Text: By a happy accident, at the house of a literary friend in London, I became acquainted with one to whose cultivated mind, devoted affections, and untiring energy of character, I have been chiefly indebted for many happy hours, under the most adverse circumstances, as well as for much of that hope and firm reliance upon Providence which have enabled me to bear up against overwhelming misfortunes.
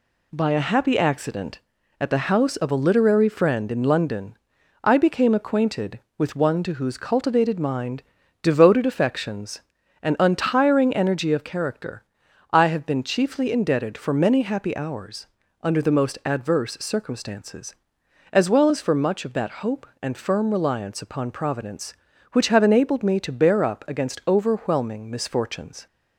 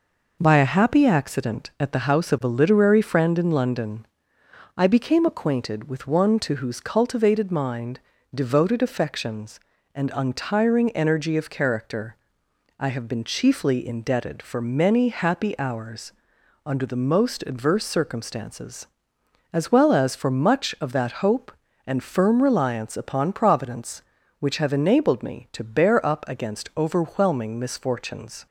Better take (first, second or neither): neither